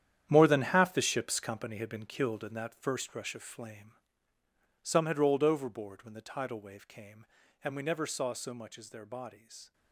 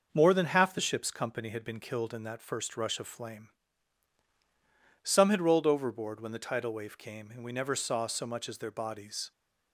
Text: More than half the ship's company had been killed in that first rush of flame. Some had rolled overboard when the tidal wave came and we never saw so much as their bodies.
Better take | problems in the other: second | gets quieter; strong; throughout; 12 dB

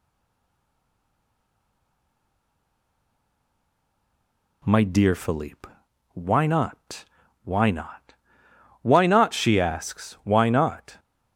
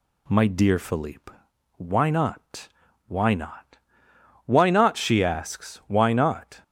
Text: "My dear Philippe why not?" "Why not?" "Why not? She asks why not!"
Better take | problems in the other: second | stays silent before the first word; strong; until 4.6 s; 4.6 s long // pauses between "Philippe" and "why"; noticeable; at 5.6 s; 0.46 s long; noticeable in the second

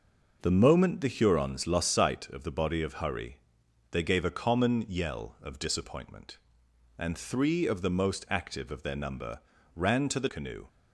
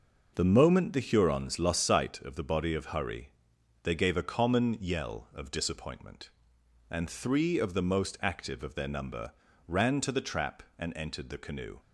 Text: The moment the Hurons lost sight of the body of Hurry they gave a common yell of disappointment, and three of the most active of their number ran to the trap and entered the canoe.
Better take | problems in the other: second | pauses between "Hurry" and "they"; noticeable; at 3.3 s; 0.54 s long; noticeable in the second // pauses between "number" and "ran"; slight; at 9.3 s; 0.34 s long; slight in the second // skips "trap and entered the"; at 10.2 s

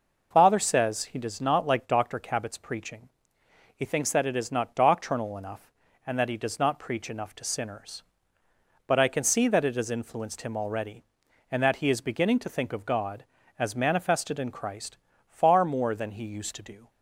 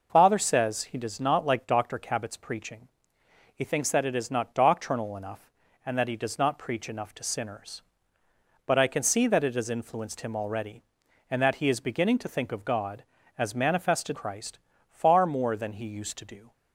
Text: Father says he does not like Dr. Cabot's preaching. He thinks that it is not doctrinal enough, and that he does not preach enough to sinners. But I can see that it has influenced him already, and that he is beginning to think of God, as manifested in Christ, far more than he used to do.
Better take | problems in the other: first | skips "in"; at 14.1 s

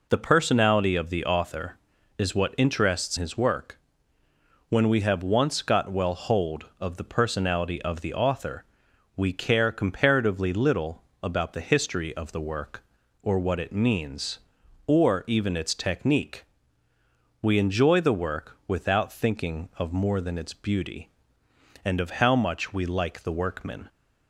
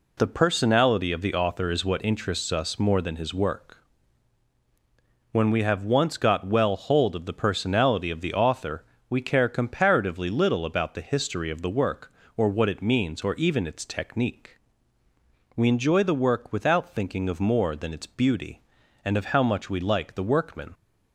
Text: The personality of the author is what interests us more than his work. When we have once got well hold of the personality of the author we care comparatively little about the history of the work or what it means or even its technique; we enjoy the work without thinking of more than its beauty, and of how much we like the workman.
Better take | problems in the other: second | skips "us more than"; at 3.1 s // pauses between "author" and "we"; noticeable; at 8.6 s; 0.52 s long; slight in the second // pauses between "little" and "about"; slight; at 11.0 s; 0.18 s long

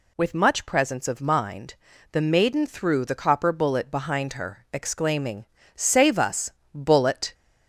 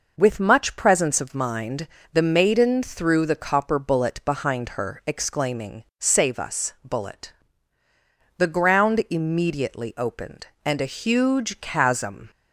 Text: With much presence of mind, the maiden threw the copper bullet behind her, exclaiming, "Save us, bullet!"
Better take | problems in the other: first | goes on to say "The ground immediately opened and a huge chasm"; strong; from 8.3 s on; 3.9 s long

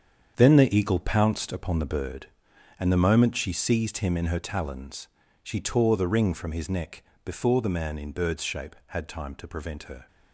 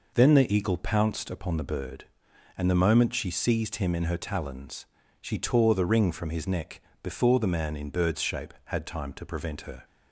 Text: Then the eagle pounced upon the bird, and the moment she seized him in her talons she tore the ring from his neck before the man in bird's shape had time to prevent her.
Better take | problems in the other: second | gets quieter; strong; throughout; 11 dB // pauses between "talons" and "she"; at 5.0 s; 0.38 s long; also in the second // pauses between "neck" and "before"; slight; at 7.0 s; 0.22 s long; slight in the second

